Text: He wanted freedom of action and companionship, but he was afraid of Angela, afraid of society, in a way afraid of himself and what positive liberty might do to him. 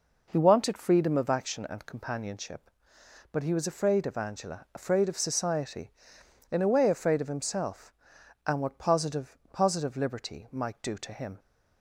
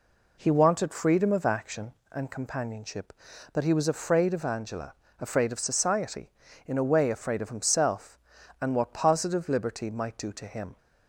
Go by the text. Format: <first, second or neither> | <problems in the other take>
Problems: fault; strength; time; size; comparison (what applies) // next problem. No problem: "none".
second | says "positive" twice; at 9.5 s